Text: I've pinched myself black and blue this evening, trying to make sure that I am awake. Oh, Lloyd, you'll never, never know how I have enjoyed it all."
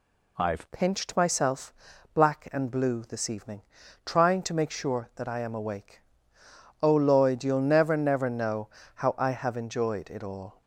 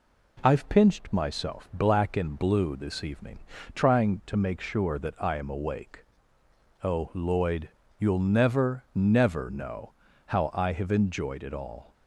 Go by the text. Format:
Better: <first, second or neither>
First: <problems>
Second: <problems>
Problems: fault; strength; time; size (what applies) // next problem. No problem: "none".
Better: second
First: changes voice at "pinched"; from 0.7 s on; 9.9 s long // pauses between "myself" and "black"; at 1.7 s; 0.40 s long // pauses between "know" and "how"; slight; at 8.6 s; 0.28 s long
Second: pauses between "know" and "how"; slight; at 9.9 s; 0.34 s long